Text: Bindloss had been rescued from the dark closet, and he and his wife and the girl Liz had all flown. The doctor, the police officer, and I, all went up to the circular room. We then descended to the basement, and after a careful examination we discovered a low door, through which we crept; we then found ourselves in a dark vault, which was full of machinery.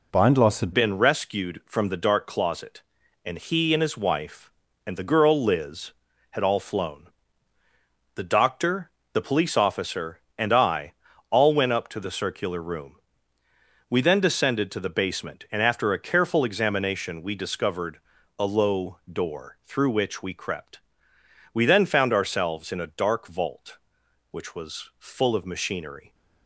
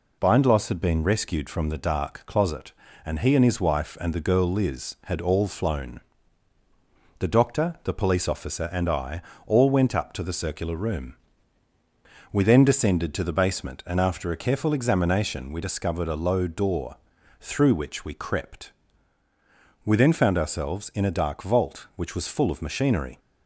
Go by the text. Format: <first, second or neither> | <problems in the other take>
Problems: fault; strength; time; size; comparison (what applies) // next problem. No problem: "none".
second | changes voice at "been"; from 0.7 s on; 25.4 s long // pauses between "discovered" and "a"; at 17.9 s; 0.40 s long